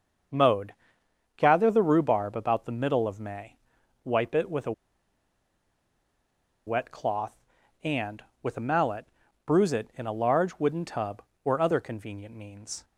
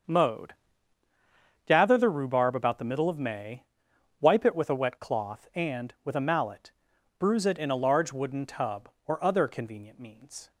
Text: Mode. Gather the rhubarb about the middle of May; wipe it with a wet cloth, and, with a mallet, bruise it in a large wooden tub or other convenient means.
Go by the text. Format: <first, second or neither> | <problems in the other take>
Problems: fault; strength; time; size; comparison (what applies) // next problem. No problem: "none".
second | starts louder than the rest; until 1.9 s; 6.5 dB; also in the second // pauses between "a" and "wet"; strong; at 4.7 s; 1.9 s long